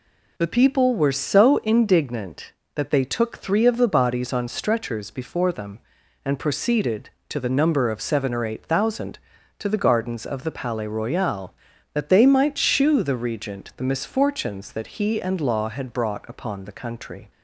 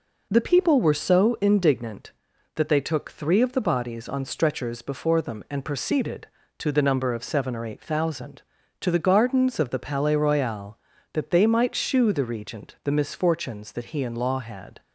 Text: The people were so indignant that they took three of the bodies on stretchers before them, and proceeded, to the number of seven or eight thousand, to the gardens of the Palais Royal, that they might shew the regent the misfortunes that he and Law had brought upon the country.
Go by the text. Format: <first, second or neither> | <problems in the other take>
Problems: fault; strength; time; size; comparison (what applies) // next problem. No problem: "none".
first | stops before "brought upon the country"; at 14.8 s